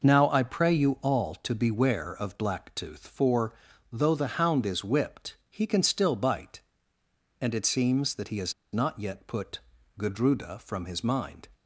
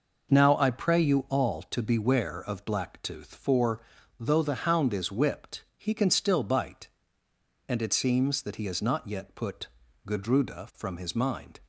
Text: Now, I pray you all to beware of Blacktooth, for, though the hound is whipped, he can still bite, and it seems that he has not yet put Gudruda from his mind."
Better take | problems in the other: second | pauses between "has" and "not"; slight; at 8.5 s; 0.20 s long // pauses between "put" and "Gudruda"; at 9.5 s; 0.40 s long; also in the second

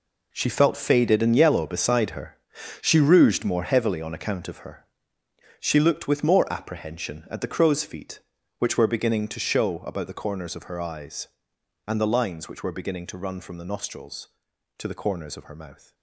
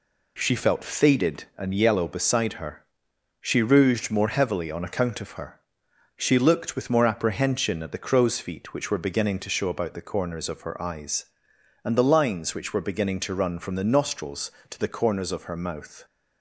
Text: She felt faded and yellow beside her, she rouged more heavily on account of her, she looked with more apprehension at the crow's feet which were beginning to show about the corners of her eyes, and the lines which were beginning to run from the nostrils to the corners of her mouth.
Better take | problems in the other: second | gets quieter; strong; throughout; 12.5 dB

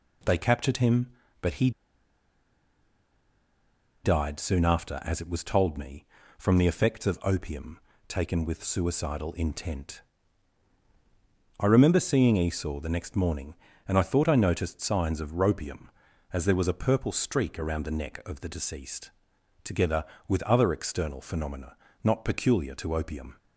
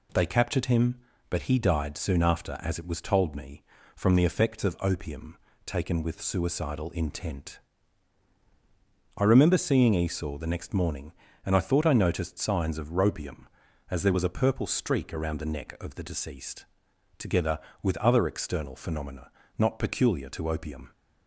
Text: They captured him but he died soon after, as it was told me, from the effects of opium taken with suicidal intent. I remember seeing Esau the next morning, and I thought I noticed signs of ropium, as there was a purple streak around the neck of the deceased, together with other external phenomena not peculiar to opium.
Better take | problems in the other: second | pauses between "he" and "died"; strong; at 1.7 s; 2.3 s long // pauses between "opium" and "taken"; slight; at 7.7 s; 0.28 s long; slight in the second // pauses between "phenomena" and "not"; slight; at 21.7 s; 0.28 s long; slight in the second

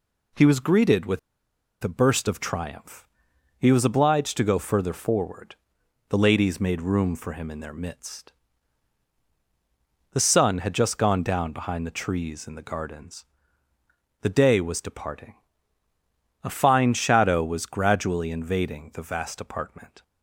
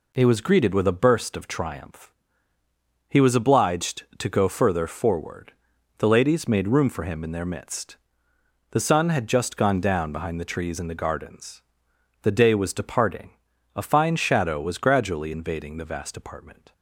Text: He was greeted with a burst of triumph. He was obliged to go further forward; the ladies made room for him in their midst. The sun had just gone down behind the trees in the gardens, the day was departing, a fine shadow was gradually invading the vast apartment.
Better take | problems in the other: second | pauses between "with" and "a"; noticeable; at 1.1 s; 0.63 s long

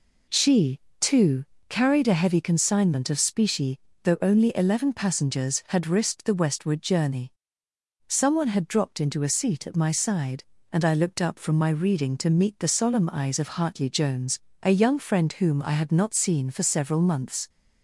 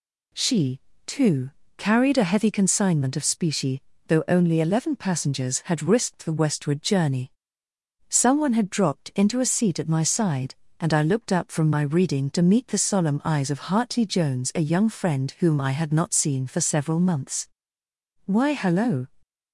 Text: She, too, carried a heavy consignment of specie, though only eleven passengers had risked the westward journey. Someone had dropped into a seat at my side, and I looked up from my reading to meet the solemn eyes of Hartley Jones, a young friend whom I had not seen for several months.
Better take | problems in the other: first | goes on to say "Why hello"; noticeable; from 18.2 s on; 0.82 s long

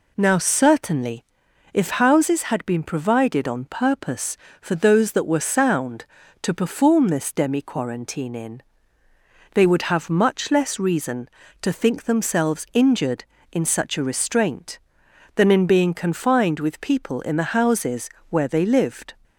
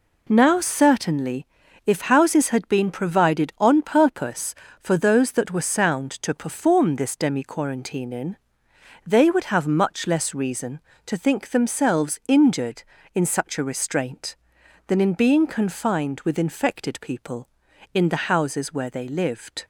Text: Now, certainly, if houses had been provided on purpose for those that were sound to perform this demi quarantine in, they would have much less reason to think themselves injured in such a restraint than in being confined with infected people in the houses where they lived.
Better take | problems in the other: second | skips "infected"; at 16.8 s // pauses between "houses" and "where"; slight; at 18.1 s; 0.18 s long

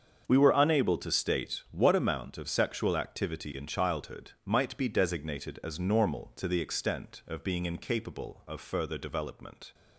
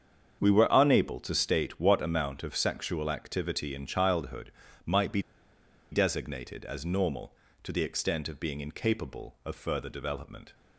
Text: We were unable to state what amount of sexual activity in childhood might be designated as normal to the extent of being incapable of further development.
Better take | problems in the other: first | starts louder than the rest; strong; until 1.4 s; 7.5 dB; also in the first // pauses between "childhood" and "might"; slight; at 4.5 s; 0.36 s long // pauses between "be" and "designated"; noticeable; at 5.2 s; 0.71 s long

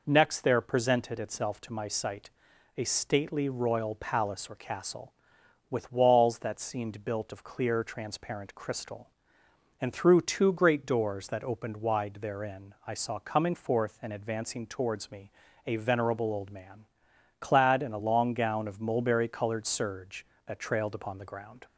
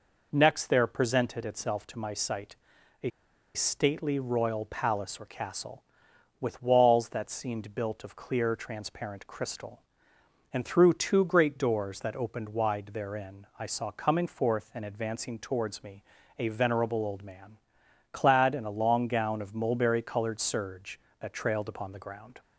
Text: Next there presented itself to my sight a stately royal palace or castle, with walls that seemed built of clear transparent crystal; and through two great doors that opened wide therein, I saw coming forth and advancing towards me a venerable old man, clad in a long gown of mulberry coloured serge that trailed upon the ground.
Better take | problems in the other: first | pauses between "sight" and "a"; noticeable; at 2.5 s; 0.46 s long; noticeable in the first // pauses between "a" and "stately"; at 3.1 s; 0.44 s long // pauses between "me" and "a"; slight; at 16.0 s; 0.34 s long; slight in the first

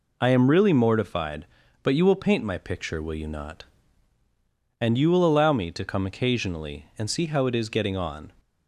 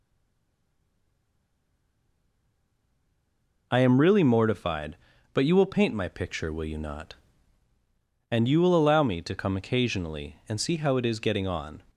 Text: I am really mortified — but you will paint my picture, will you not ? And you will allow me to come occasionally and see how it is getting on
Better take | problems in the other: first | stays silent before the first word; strong; until 3.7 s; 3.7 s long

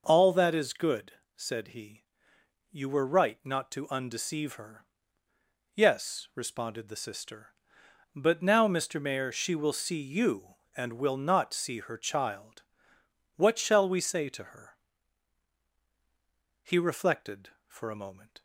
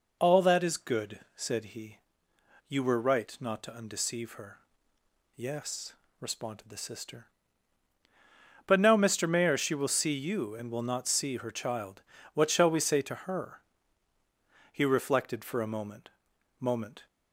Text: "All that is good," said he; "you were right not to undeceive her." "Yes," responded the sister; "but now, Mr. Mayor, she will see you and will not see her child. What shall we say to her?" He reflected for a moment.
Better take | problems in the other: first | says "moment" twice; at 16.6 s

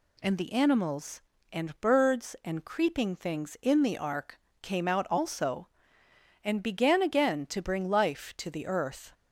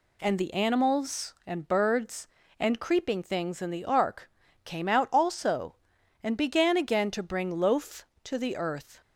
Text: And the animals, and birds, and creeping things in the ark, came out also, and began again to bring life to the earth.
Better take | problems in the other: first | says "loaf" for "life"; at 7.5 s

